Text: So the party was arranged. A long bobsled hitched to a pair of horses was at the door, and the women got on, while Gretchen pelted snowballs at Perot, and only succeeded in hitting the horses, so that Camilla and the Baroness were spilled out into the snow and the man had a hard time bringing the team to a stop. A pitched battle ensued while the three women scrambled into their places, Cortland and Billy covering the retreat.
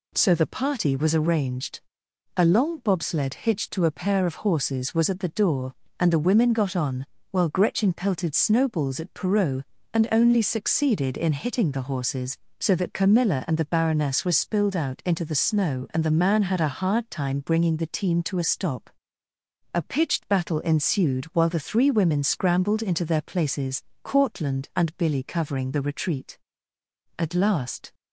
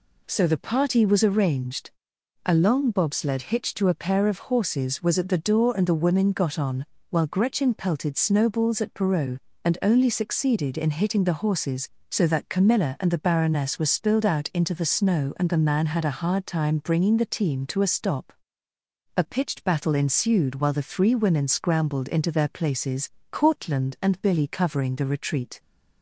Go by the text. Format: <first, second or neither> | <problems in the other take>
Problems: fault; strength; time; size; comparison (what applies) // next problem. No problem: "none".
second | goes on to say "At last"; noticeable; from 27.1 s on; 0.76 s long